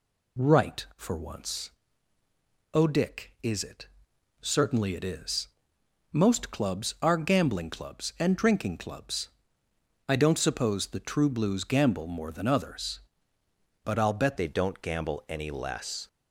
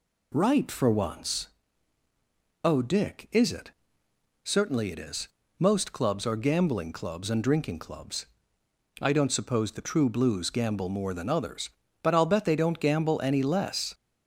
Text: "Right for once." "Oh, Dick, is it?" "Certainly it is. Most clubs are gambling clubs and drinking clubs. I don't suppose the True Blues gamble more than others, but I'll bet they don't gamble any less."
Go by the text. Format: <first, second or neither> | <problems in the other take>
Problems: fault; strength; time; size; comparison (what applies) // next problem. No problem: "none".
second | changes voice at "they"; from 14.3 s on; 1.7 s long